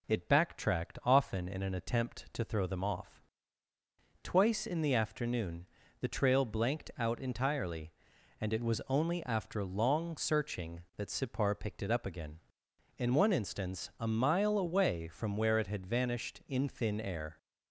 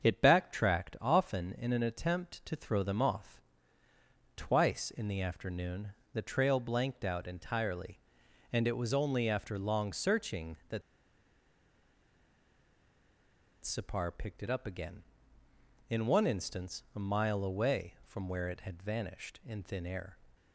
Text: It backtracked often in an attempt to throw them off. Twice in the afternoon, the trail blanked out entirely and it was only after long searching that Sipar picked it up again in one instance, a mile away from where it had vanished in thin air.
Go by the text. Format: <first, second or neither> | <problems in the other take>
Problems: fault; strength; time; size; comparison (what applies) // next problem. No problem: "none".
first | starts louder than the rest; until 1.0 s; 7 dB // pauses between "that" and "Sipar"; strong; at 10.8 s; 2.8 s long